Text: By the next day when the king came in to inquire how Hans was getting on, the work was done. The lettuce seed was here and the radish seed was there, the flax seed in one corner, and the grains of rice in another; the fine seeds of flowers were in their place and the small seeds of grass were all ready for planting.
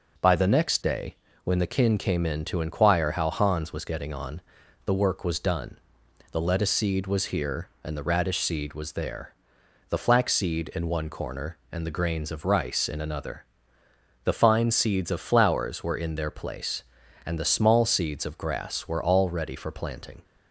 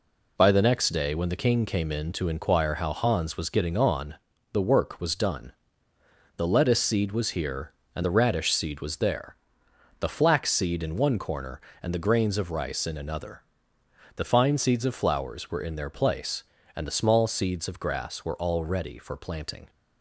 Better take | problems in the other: second | pauses between "day" and "when"; slight; at 1.1 s; 0.28 s long // says "kin" for "king"; at 1.6 s

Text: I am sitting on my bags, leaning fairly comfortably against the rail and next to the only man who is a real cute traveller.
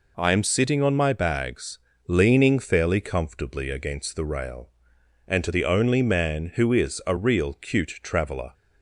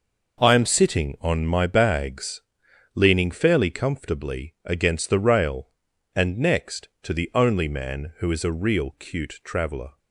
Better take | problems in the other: second | skips "next"; at 5.4 s

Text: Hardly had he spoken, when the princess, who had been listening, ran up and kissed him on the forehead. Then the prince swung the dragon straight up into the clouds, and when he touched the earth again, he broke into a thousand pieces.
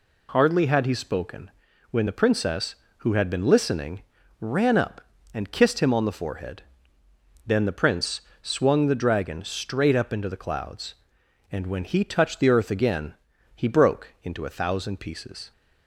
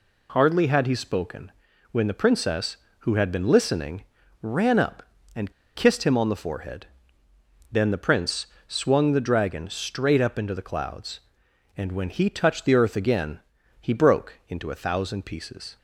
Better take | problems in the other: first | pauses between "and" and "kissed"; slight; at 5.5 s; 0.22 s long // pauses between "prince" and "swung"; slight; at 8.4 s; 0.22 s long; slight in the first

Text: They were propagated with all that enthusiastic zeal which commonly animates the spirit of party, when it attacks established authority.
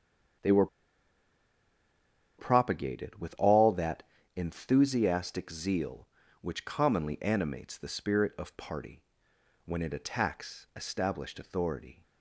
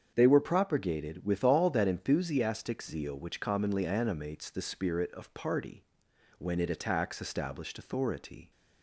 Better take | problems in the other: second | starts louder than the rest; until 3.1 s; 6.5 dB; strong in the second // pauses between "were" and "propagated"; strong; at 0.6 s; 1.7 s long // pauses between "that" and "enthusiastic"; slight; at 4.0 s; 0.32 s long

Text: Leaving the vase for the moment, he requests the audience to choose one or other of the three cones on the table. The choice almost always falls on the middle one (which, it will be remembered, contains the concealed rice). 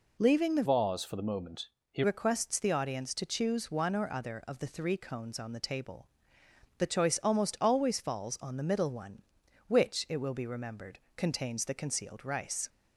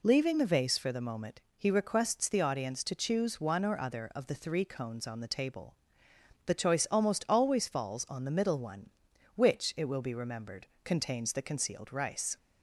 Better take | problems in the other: second | changes voice from "vase" to "he"; from 0.6 to 2.0 s; 1.4 s long

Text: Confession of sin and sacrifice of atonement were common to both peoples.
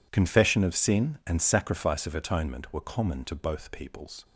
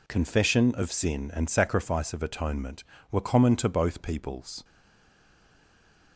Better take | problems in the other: first | stays silent after the last word; noticeable; from 4.6 s on; 1.5 s long

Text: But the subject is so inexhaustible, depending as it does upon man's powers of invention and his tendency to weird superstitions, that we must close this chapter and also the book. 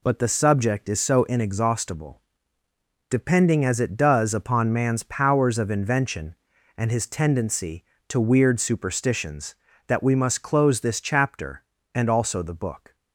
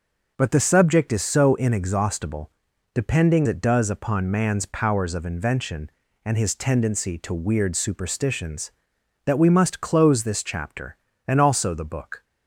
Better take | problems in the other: first | skips "as"; at 3.4 s

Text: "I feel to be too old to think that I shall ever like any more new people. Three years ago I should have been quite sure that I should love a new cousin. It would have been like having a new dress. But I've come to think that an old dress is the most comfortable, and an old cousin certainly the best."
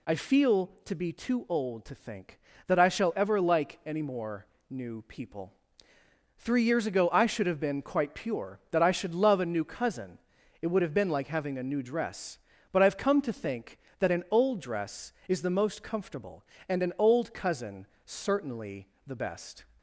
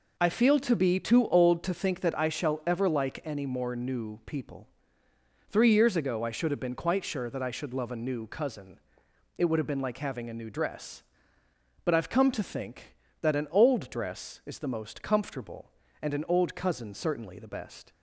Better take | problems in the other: second | pauses between "more" and "new"; slight; at 4.4 s; 0.22 s long // says "pure" for "sure"; at 8.1 s // pauses between "cousin" and "certainly"; slight; at 17.8 s; 0.18 s long // pauses between "certainly" and "the"; slight; at 18.8 s; 0.20 s long

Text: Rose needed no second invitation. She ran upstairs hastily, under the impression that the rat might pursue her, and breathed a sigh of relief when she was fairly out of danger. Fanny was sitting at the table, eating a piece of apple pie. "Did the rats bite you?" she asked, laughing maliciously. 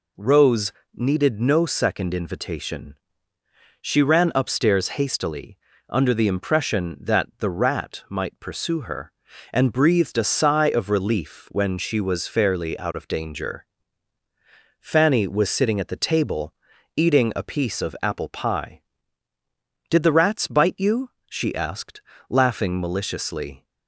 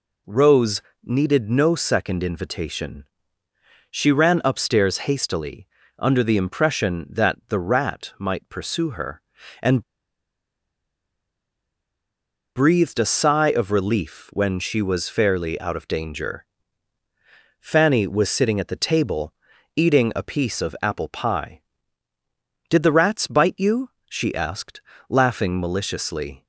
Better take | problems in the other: first | pauses between "Rose" and "needed"; slight; at 0.8 s; 0.22 s long; slight in the first // pauses between "and" and "breathed"; strong; at 9.8 s; 2.7 s long

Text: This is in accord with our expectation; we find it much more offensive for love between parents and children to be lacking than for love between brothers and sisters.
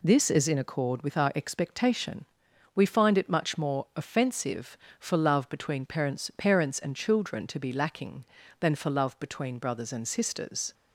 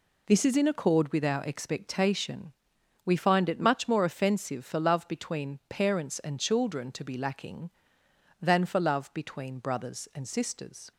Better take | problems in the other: second | says "parents" twice; at 6.3 s

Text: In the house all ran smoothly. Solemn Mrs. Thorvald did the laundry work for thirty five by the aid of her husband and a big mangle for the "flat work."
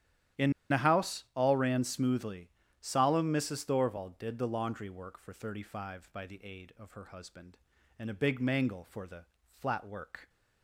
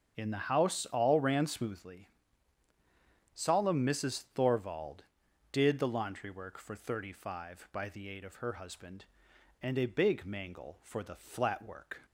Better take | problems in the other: second | starts louder than the rest; strong; until 1.6 s; 10.5 dB; strong in the second // pauses between "In" and "the"; slight; at 0.5 s; 0.18 s long // pauses between "the" and "flat"; slight; at 9.2 s; 0.28 s long

